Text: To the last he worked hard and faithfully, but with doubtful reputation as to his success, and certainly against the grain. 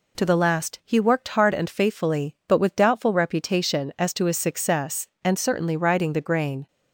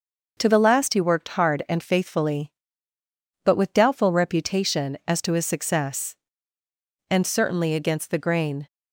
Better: second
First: says "riding" for "against"; at 5.7 s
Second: none

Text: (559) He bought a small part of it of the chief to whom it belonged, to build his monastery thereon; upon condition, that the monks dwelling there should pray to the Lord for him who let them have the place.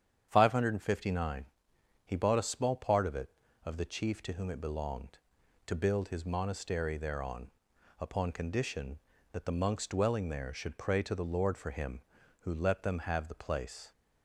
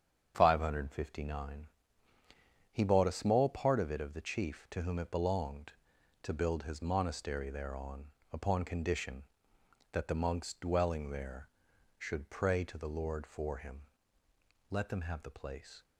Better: first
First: starts louder than the rest; strong; until 1.3 s; 8.5 dB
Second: starts louder than the rest; strong; until 1.3 s; 7.5 dB // skips "who"; at 14.2 s

